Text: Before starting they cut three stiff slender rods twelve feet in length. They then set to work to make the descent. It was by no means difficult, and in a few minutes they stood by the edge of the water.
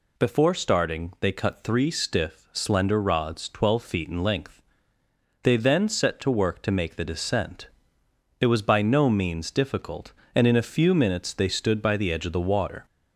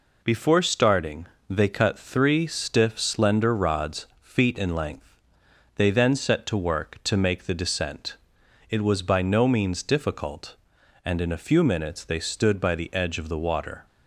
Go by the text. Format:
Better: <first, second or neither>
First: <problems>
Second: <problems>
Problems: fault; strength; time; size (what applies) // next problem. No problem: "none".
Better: first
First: none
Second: pauses between "starting" and "they"; slight; at 1.2 s; 0.24 s long // skips "twelve"; at 4.1 s